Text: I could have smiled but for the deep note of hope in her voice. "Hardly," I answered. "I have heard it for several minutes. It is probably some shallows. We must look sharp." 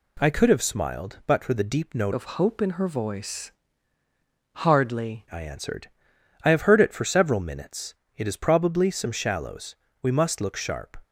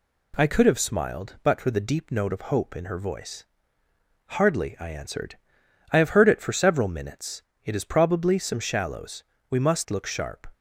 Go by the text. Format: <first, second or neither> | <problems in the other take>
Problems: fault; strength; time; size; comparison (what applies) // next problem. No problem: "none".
second | changes voice from "of" to "Hardly"; from 2.1 to 5.2 s; 3.1 s long